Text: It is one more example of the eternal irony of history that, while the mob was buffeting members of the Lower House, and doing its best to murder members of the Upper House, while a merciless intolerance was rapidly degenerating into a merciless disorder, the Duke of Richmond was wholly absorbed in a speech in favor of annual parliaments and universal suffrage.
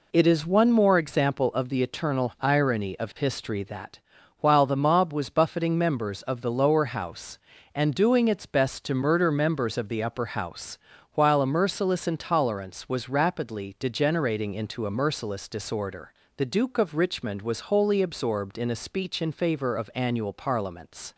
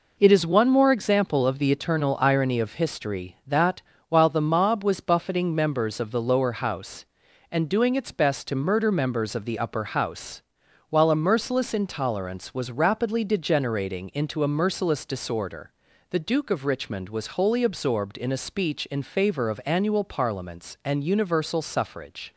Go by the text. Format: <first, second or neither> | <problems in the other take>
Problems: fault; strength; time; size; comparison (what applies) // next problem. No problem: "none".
second | stops before "and universal suffrage"; at 21.1 s